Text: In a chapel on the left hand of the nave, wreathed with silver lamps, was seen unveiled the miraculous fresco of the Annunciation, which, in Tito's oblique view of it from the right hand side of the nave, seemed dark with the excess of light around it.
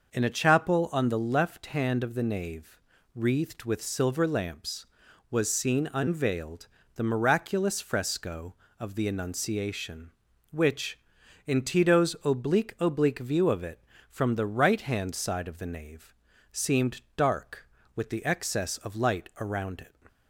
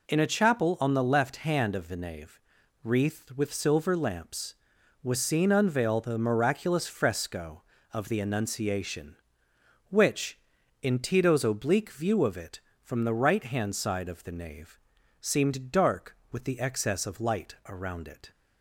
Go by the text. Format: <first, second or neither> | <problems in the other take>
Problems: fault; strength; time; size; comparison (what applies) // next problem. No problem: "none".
second | pauses between "unveiled" and "the"; slight; at 6.6 s; 0.28 s long // says "oblique" twice; at 12.8 s // pauses between "seemed" and "dark"; slight; at 17.0 s; 0.16 s long